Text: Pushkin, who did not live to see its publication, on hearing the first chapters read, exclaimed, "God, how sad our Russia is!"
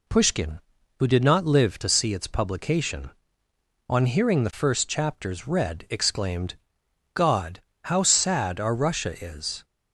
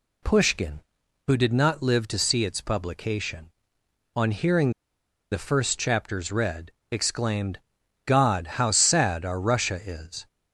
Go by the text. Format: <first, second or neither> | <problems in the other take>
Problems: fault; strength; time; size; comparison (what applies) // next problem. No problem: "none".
first | pauses between "hearing" and "the"; noticeable; at 4.7 s; 0.60 s long